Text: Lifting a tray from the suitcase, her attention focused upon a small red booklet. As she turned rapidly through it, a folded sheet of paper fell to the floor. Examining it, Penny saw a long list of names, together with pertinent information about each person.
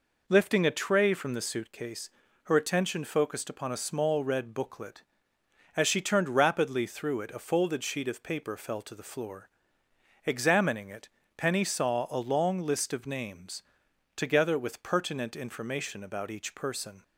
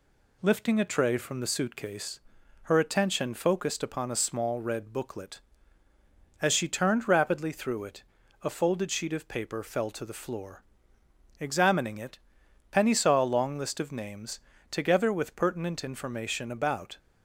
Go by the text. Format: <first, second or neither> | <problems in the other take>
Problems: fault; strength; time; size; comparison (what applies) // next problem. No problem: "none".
first | stops before "each person"; at 16.9 s